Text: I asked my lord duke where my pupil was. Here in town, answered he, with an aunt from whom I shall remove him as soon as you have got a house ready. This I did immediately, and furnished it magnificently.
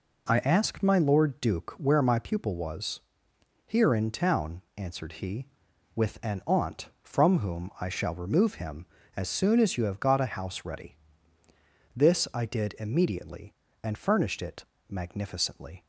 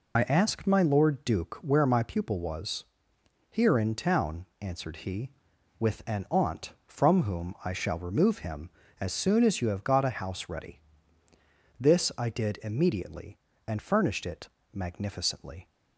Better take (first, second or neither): first